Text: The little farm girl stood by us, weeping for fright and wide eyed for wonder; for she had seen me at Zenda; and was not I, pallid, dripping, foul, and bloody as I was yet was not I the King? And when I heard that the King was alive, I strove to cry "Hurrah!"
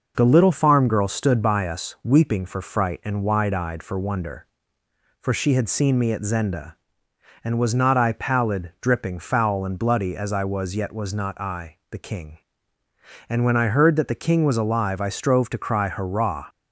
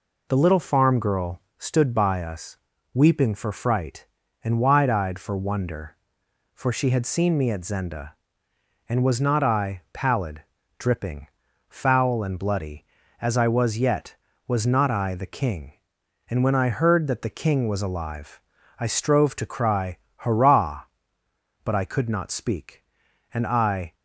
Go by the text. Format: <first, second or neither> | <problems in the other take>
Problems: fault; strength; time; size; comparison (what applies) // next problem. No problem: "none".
first | pauses between "girl" and "stood"; slight; at 1.3 s; 0.18 s long // pauses between "cry" and "Hurrah"; slight; at 19.9 s; 0.22 s long // goes on to say "But I could not speak and I"; strong; from 21.6 s on; 2.3 s long